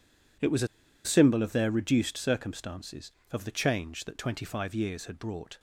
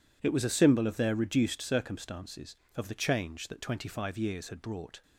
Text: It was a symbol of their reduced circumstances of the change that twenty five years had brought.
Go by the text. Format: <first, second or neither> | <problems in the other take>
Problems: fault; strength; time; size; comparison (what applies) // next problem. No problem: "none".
second | pauses between "a" and "symbol"; at 0.6 s; 0.38 s long